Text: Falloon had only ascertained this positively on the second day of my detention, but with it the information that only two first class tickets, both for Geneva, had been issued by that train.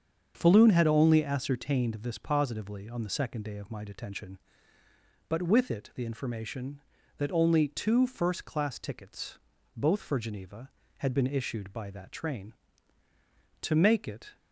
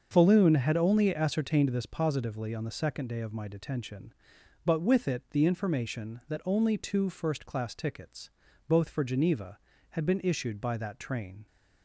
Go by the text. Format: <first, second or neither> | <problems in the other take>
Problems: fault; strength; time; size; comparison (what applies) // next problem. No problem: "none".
second | starts louder than the rest; until 1.3 s; 7 dB; also in the second // goes on to say "To make it"; noticeable; from 13.6 s on; 0.74 s long